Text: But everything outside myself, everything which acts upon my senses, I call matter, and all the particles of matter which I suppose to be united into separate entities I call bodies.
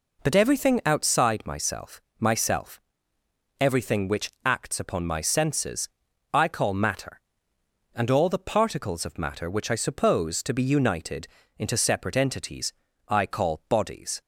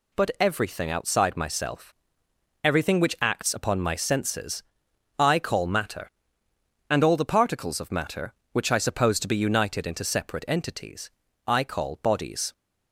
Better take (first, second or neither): second